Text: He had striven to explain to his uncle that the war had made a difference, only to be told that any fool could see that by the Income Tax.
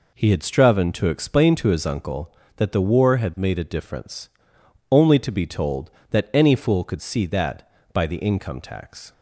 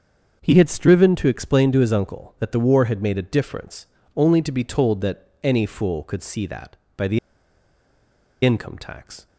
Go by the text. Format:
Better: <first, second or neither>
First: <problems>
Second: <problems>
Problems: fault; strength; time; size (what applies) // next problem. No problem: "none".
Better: first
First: none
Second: starts louder than the rest; until 1.4 s; 7 dB // pauses between "that" and "any"; slight; at 5.2 s; 0.16 s long // pauses between "the" and "Income"; strong; at 7.1 s; 1.2 s long